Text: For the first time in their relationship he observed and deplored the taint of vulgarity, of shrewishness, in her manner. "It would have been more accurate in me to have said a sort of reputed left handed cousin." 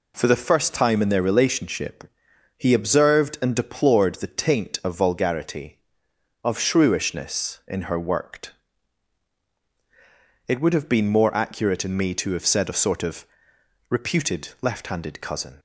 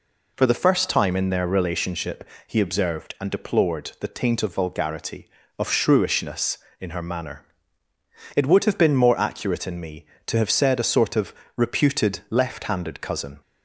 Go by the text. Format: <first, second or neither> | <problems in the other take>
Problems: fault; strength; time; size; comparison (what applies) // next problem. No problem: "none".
second | pauses between "relationship" and "he"; noticeable; at 2.0 s; 0.52 s long; slight in the second // says "worked" for "manner"; at 7.9 s // pauses between "of" and "reputed"; noticeable; at 13.2 s; 0.64 s long; slight in the second